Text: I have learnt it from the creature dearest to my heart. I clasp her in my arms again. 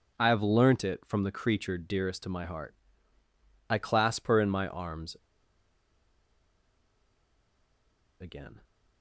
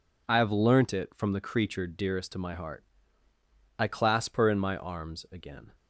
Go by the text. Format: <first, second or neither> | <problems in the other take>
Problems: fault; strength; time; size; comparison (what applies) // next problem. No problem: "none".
second | pauses between "arms" and "again"; strong; at 5.1 s; 3.0 s long